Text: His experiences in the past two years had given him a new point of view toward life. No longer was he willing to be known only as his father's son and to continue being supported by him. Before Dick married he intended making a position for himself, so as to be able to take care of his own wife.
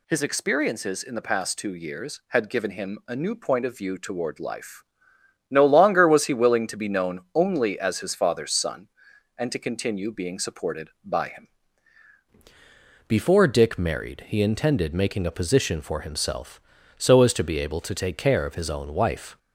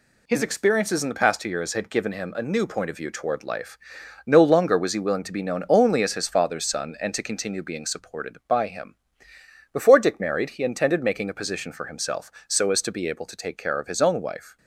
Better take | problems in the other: second | changes voice at "Before"; from 13.0 s on; 6.3 s long

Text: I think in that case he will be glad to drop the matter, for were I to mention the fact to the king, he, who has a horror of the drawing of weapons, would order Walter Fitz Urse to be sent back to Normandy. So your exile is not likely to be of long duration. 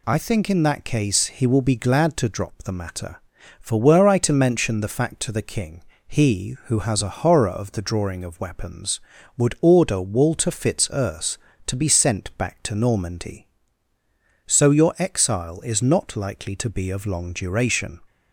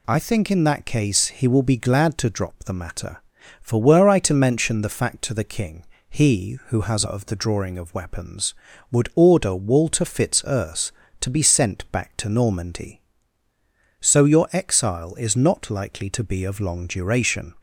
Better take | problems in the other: first | skips "a horror"; at 7.0 s

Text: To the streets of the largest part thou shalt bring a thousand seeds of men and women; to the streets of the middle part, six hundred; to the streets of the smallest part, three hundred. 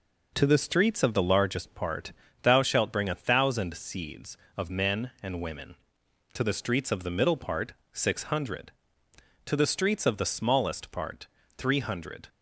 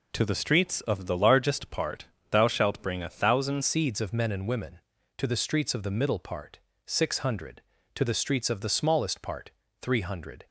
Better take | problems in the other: first | pauses between "part" and "thou"; slight; at 2.0 s; 0.24 s long; slight in the first // changes voice at "seeds"; from 3.6 s on; 6.8 s long

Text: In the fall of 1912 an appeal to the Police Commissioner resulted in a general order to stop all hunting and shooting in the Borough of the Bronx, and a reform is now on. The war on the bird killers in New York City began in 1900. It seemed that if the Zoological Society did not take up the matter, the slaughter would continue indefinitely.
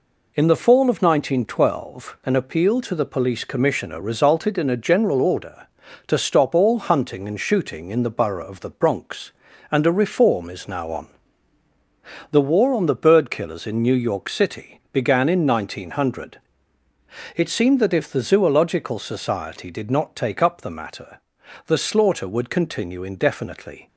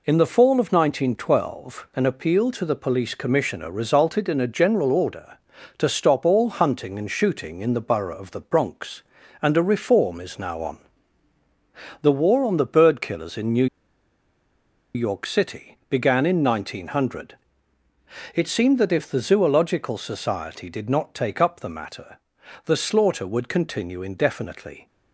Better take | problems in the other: first | pauses between "New" and "York"; strong; at 13.6 s; 1.2 s long

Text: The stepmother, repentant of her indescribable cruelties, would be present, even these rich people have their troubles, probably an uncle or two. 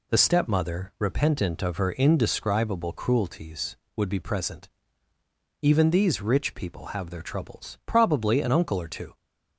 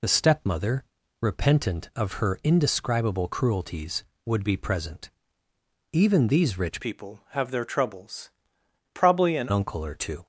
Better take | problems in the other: first | changes voice from "people" to "an"; from 6.8 to 9.4 s; 2.6 s long

